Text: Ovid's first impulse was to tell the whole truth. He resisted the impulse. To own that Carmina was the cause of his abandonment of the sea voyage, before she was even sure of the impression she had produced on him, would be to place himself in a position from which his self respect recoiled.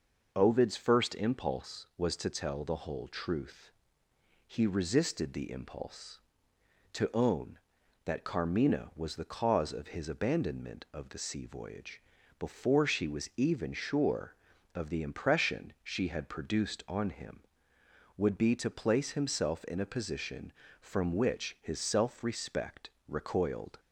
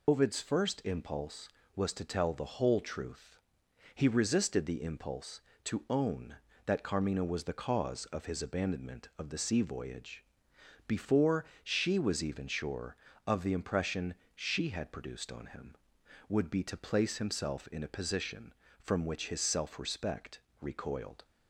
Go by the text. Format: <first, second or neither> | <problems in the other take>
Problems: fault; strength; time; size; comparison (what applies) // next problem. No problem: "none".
first | loses the start of "Ovid's"; at 0.0 s; 85 ms // pauses between "before" and "she"; slight; at 11.4 s; 0.20 s long // pauses between "impression" and "she"; slight; at 14.1 s; 0.18 s long // pauses between "respect" and "recoiled"; slight; at 20.3 s; 0.22 s long; slight in the first